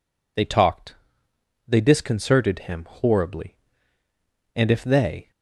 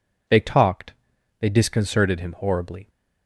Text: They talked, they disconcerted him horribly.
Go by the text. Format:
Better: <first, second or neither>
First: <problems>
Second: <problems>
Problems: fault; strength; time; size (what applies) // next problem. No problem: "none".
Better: second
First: goes on to say "And if they"; noticeable; from 4.5 s on; 0.76 s long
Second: none